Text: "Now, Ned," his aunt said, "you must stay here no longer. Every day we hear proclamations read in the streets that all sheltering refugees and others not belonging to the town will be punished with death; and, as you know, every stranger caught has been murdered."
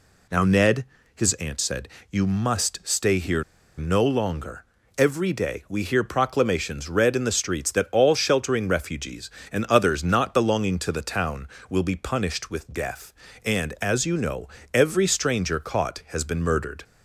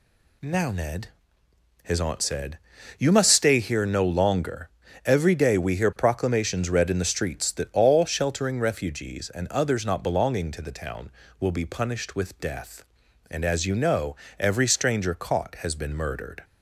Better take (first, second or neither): second